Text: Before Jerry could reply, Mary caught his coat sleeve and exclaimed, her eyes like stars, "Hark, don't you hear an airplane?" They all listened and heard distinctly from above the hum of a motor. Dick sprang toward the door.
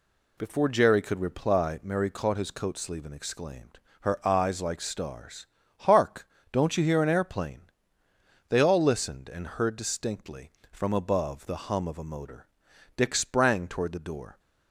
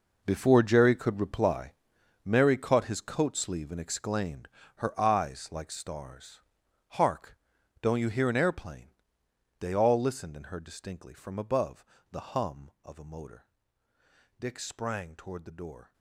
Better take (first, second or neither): first